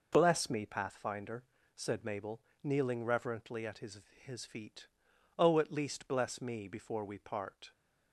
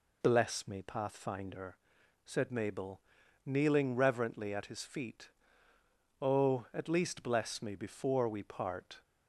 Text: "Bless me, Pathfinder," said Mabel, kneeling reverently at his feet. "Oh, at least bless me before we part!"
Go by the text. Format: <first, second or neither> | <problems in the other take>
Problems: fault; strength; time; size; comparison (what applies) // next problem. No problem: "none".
second | says "his" twice; at 4.2 s